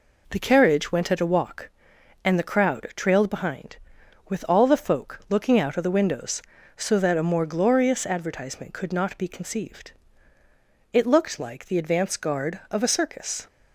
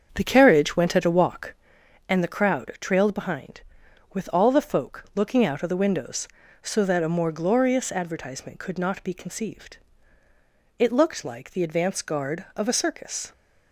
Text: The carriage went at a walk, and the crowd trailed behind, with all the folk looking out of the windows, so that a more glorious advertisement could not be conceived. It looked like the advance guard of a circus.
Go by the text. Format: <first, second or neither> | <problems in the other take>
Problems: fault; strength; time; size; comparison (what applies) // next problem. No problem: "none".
first | starts louder than the rest; until 1.7 s; 7 dB